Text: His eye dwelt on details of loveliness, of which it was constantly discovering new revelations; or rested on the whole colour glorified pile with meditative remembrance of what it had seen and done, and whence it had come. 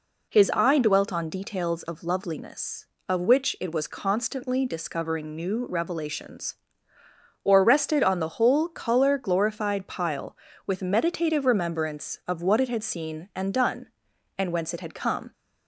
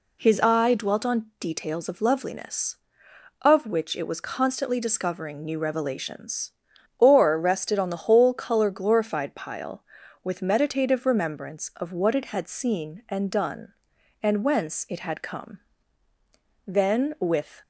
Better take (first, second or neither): first